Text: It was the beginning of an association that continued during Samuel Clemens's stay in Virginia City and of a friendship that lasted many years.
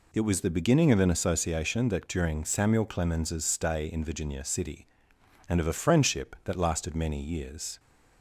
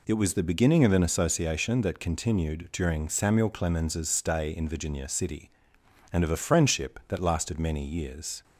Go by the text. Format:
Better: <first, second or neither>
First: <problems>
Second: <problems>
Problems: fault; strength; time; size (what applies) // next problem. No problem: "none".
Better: second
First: skips "continued"; at 2.0 s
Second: none